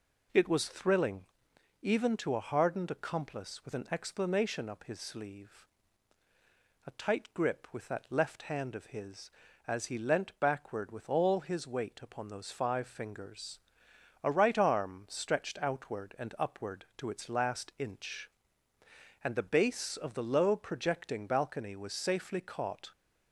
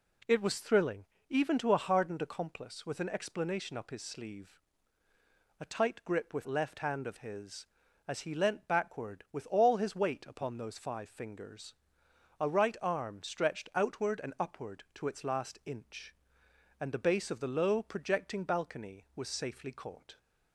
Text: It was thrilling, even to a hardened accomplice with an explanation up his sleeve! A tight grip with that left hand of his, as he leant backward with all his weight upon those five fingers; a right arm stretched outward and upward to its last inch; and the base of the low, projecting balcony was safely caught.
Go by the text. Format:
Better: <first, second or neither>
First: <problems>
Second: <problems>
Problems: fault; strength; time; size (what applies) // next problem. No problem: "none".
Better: first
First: none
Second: skips "that"; at 6.4 s